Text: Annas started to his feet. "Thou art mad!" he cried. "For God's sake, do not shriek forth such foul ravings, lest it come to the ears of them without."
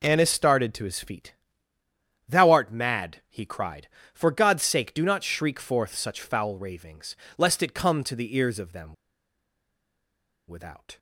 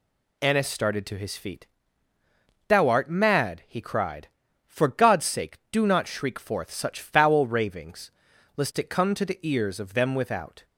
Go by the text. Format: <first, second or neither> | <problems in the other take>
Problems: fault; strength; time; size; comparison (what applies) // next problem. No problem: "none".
second | pauses between "them" and "without"; strong; at 8.9 s; 1.5 s long